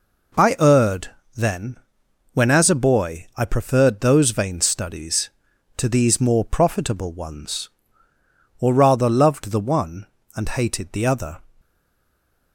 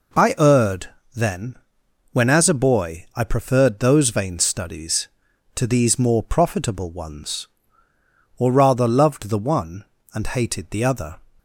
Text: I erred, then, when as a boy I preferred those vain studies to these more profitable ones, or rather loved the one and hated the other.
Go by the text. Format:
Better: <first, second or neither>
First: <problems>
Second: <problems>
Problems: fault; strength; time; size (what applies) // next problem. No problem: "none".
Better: second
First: stays silent after the last word; slight; from 11.6 s on; 0.9 s long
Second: none